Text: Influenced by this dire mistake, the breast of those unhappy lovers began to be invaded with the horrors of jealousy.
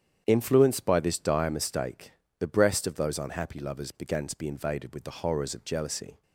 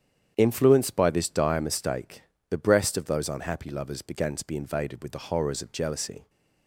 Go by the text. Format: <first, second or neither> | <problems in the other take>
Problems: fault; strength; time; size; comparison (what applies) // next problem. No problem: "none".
neither | starts louder than the rest; strong; the same in both